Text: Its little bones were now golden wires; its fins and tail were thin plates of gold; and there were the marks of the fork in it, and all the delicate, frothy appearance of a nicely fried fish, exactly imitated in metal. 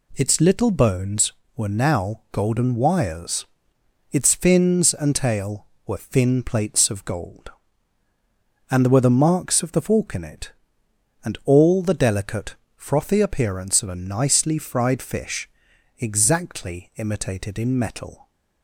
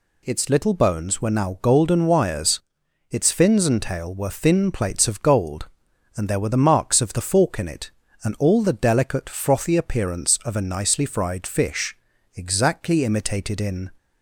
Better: first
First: none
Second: stops before "metal"; at 13.9 s

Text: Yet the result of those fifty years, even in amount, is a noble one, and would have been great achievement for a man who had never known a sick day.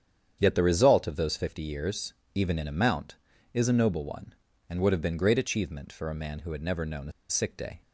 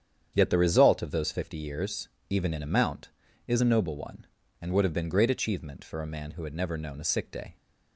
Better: second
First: starts louder than the rest; strong; until 1.4 s; 8.5 dB // pauses between "a" and "sick"; slight; at 7.1 s; 0.17 s long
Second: starts louder than the rest; strong; until 1.3 s; 8.5 dB

